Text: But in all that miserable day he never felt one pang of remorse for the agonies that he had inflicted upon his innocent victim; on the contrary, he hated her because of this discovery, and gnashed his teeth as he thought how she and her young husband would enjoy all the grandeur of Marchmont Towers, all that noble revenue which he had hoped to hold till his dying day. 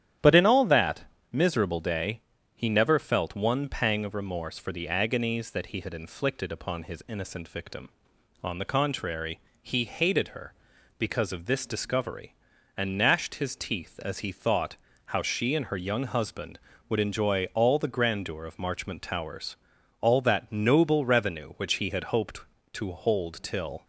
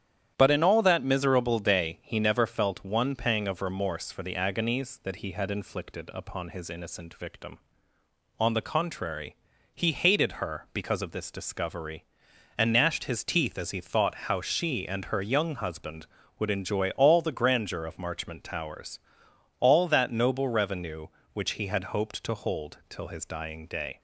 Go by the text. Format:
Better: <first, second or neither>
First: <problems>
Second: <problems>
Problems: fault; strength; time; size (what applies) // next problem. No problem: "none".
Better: second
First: starts louder than the rest; strong; until 1.4 s; 10.5 dB // pauses between "that" and "miserable"; slight; at 1.0 s; 0.28 s long // pauses between "day" and "he"; slight; at 2.2 s; 0.34 s long // pauses between "thought" and "how"; slight; at 14.7 s; 0.30 s long // stops before "his dying day"; at 23.8 s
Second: starts louder than the rest; strong; until 1.3 s; 10.5 dB